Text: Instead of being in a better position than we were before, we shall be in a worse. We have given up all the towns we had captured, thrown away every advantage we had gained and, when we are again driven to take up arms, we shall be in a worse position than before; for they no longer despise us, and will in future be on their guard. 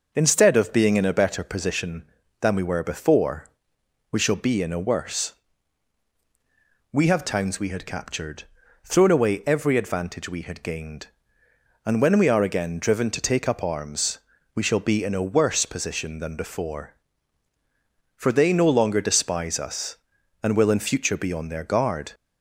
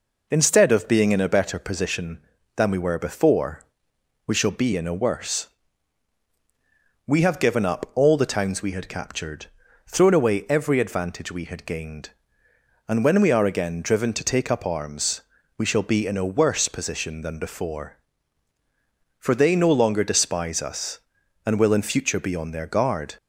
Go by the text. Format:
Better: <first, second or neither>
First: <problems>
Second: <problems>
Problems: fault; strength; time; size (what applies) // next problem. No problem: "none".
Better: second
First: skips "given up all the"; at 7.2 s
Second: none